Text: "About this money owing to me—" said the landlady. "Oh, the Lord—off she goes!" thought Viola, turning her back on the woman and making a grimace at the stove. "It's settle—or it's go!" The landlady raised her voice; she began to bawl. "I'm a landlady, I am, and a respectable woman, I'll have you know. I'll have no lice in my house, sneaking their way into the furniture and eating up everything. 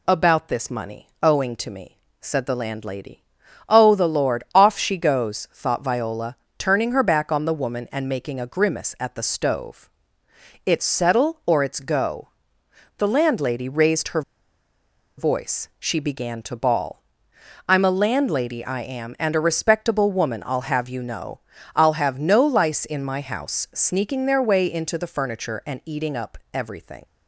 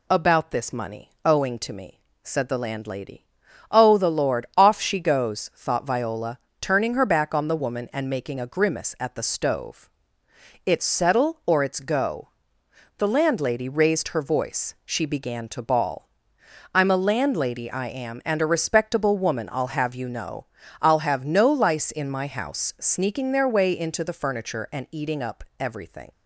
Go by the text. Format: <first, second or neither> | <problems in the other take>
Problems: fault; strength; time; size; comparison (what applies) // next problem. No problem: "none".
second | pauses between "money" and "owing"; slight; at 1.0 s; 0.16 s long; slight in the second // pauses between "her" and "voice"; noticeable; at 14.2 s; 0.96 s long // pauses between "up" and "everything"; slight; at 26.3 s; 0.16 s long; slight in the second